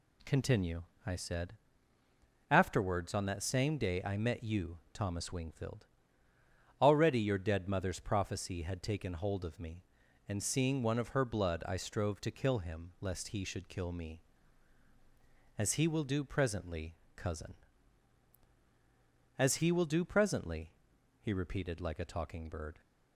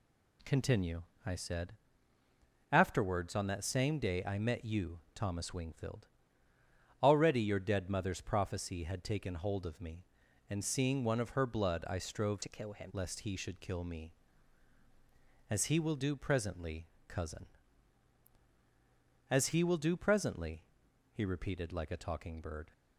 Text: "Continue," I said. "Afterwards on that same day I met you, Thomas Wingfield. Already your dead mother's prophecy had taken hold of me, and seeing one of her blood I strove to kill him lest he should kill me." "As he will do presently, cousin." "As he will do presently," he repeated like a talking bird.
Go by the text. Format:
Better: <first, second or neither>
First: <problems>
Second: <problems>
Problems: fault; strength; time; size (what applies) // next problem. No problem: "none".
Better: first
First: none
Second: changes voice from "to" to "him"; from 12.4 to 12.9 s; 0.5 s long